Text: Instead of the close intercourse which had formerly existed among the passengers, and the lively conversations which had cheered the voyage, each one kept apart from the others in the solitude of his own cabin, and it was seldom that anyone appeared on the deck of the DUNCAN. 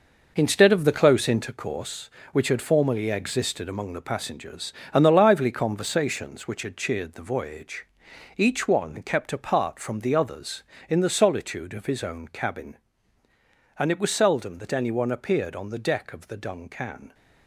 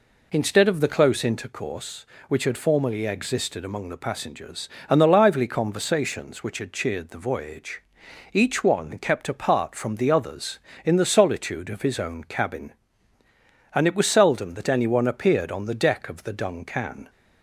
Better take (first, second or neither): second